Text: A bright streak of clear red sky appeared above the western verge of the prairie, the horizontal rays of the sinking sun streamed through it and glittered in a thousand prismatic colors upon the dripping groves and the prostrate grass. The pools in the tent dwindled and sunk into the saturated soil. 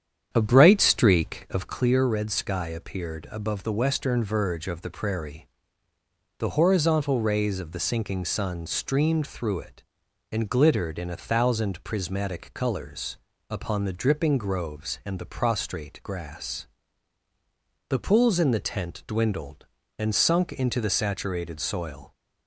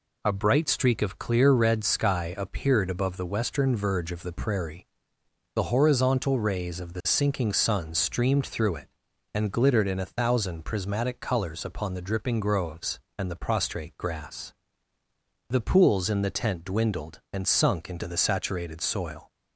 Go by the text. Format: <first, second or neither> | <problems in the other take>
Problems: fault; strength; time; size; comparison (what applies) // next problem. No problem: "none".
second | starts louder than the rest; strong; until 1.9 s; 8.5 dB // pauses between "colors" and "upon"; slight; at 13.1 s; 0.32 s long